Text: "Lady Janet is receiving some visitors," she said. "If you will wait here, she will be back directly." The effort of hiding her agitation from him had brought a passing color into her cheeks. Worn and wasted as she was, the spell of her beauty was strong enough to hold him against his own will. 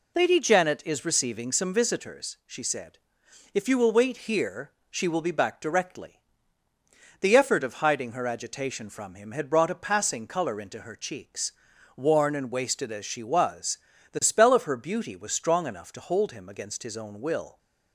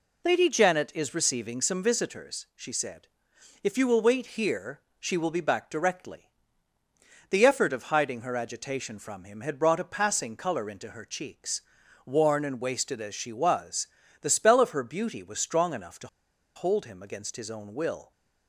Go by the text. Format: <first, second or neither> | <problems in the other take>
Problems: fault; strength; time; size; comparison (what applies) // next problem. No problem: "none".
first | pauses between "to" and "hold"; noticeable; at 16.0 s; 0.49 s long